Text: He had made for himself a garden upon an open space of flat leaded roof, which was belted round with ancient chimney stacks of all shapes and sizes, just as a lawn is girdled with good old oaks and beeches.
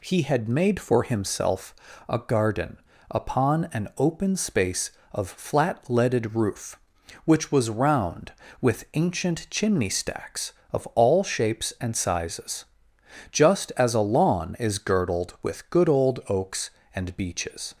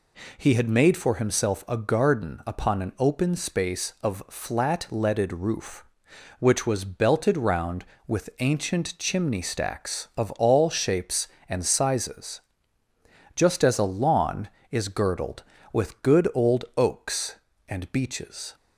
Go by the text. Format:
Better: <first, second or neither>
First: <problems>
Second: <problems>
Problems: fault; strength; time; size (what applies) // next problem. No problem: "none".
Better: second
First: pauses between "himself" and "a"; slight; at 1.7 s; 0.34 s long // pauses between "garden" and "upon"; slight; at 2.7 s; 0.34 s long // skips "belted"; at 7.6 s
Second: none